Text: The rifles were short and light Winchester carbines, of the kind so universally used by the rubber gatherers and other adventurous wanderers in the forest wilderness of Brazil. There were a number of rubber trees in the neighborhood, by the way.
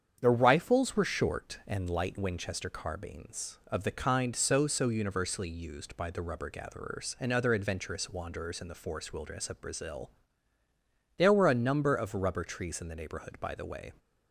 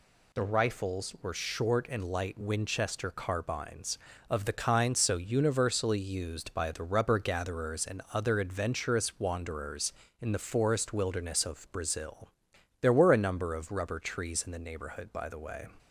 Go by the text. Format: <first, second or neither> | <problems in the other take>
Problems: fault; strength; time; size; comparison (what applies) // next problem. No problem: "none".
second | starts louder than the rest; strong; until 1.2 s; 8 dB // says "so" twice; at 4.6 s